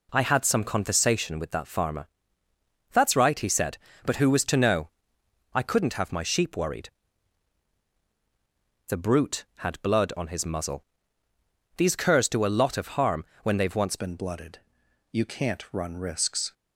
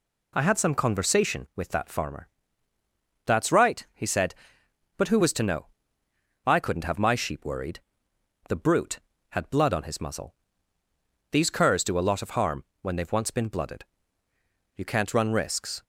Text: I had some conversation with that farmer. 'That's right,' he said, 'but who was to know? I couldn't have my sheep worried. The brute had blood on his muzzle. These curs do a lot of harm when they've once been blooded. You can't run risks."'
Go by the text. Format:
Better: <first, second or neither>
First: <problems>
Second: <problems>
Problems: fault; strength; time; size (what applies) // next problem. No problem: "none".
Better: second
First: pauses between "harm" and "when"; slight; at 13.2 s; 0.20 s long // changes voice at "been"; from 13.9 s on; 2.6 s long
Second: pauses between "harm" and "when"; slight; at 12.6 s; 0.16 s long